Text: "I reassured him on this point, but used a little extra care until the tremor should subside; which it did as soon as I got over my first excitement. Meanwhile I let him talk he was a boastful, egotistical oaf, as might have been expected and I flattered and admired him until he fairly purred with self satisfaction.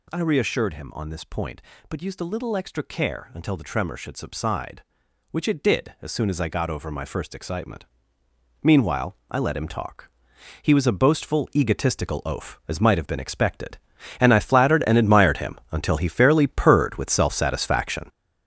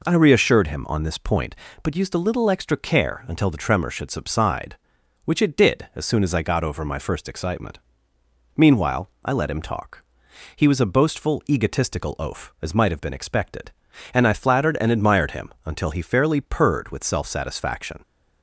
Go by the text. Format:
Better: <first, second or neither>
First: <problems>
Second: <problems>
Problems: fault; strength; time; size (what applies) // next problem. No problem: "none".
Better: second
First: gets louder; strong; throughout; 8 dB // pauses between "talk" and "he"; noticeable; at 10.0 s; 0.54 s long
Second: pauses between "talk" and "he"; noticeable; at 10.0 s; 0.54 s long